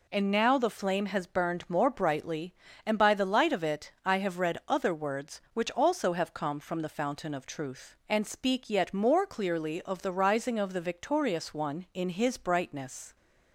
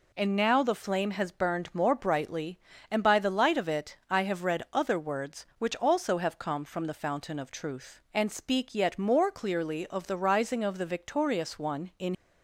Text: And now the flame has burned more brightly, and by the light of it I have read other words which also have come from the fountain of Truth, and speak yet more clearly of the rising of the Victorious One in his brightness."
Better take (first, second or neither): first